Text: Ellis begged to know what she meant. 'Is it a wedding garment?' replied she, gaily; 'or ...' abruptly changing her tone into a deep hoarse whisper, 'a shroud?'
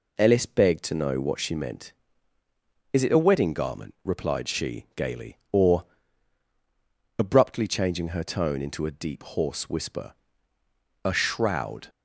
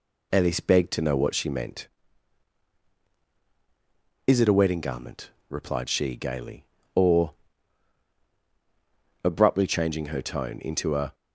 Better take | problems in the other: first | stops before "deep hoarse whisper a shroud"; at 11.1 s

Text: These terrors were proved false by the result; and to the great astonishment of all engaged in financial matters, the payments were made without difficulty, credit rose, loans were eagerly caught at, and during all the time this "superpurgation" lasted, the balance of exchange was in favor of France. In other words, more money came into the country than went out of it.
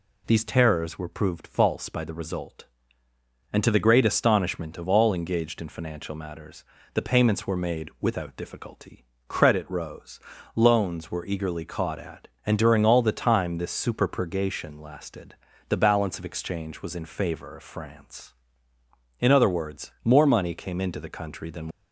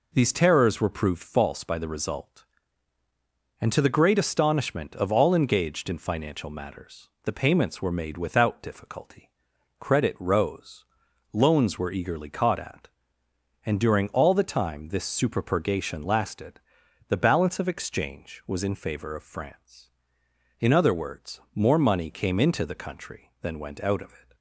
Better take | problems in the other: second | stops before "went out of it"; at 21.7 s

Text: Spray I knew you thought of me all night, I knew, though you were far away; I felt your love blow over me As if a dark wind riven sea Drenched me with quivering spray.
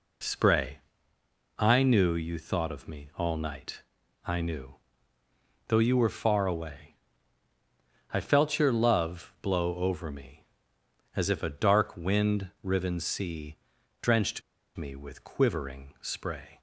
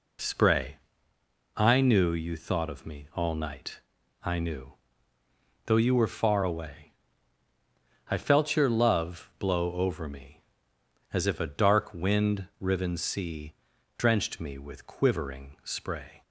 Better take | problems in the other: second | pauses between "Spray" and "I"; noticeable; at 0.7 s; 0.80 s long; noticeable in the second // pauses between "sea" and "Drenched"; at 13.5 s; 0.44 s long; also in the second // pauses between "Drenched" and "me"; slight; at 14.4 s; 0.35 s long

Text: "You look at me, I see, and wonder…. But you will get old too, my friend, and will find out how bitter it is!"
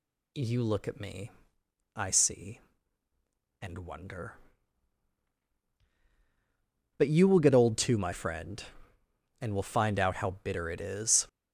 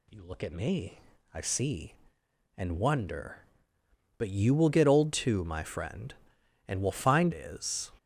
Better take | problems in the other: first | skips "out how bitter it"; at 7.3 s

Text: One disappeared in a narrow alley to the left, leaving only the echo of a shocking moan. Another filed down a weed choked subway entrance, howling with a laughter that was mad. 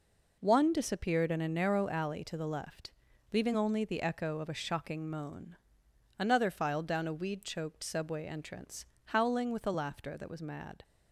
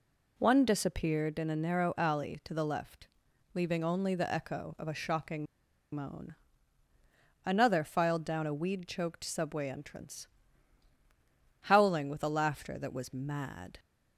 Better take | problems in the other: first | pauses between "shocking" and "moan"; noticeable; at 5.4 s; 0.49 s long

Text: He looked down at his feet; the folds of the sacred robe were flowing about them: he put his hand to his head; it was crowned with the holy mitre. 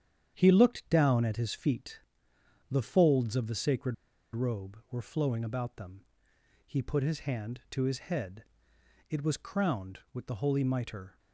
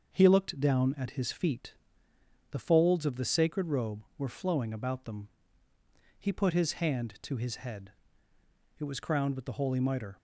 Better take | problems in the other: second | starts louder than the rest; strong; until 1.3 s; 9 dB; also in the second // pauses between "sacred" and "robe"; at 3.9 s; 0.39 s long

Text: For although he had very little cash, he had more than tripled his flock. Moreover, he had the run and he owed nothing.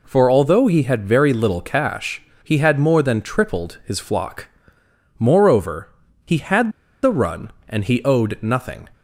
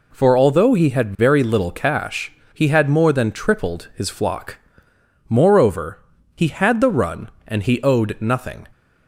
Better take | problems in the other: second | pauses between "had" and "the"; slight; at 6.7 s; 0.32 s long

